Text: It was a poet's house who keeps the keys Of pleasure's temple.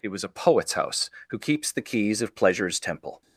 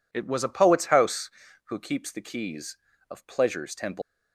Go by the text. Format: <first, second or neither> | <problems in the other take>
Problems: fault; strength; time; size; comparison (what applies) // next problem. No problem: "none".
first | leaves "temple" unfinished; at 4.0 s; 150 ms